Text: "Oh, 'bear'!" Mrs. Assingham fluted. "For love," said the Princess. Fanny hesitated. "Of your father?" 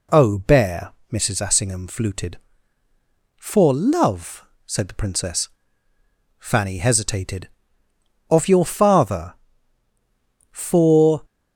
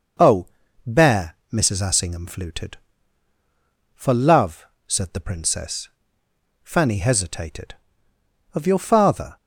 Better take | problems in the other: second | goes on to say "For"; noticeable; from 10.5 s on; 0.72 s long

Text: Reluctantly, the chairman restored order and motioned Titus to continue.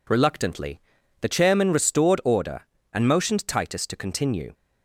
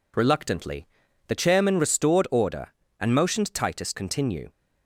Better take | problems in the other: first | skips "to"; at 3.9 s

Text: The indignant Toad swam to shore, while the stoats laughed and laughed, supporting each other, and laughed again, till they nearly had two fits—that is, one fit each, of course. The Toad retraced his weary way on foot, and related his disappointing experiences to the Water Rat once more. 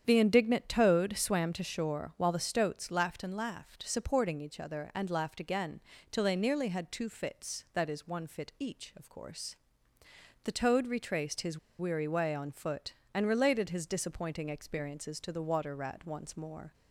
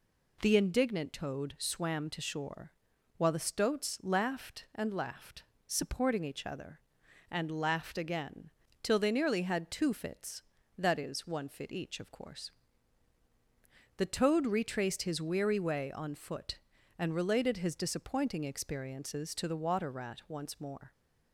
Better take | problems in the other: second | starts louder than the rest; strong; until 1.0 s; 8.5 dB // pauses between "his" and "weary"; slight; at 11.5 s; 0.21 s long

